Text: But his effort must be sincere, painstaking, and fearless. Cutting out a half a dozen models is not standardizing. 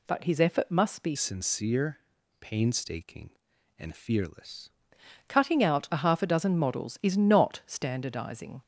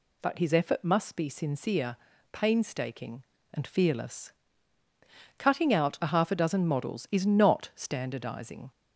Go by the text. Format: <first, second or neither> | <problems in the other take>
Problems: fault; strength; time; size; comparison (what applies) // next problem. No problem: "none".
second | changes voice from "sincere" to "fearless"; from 1.1 to 4.6 s; 3.5 s long